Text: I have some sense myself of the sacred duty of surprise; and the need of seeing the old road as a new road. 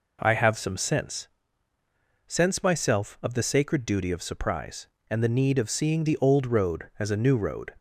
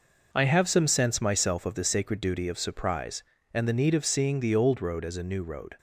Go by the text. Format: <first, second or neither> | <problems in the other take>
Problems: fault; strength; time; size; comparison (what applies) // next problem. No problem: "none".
second | says "sense" twice; at 2.2 s